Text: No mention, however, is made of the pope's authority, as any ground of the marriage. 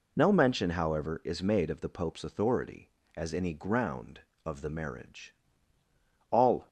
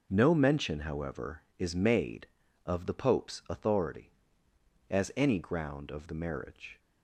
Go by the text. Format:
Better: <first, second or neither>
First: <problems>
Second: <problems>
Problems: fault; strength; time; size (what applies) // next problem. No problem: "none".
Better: second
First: goes on to say "All"; slight; from 6.2 s on; 0.38 s long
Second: none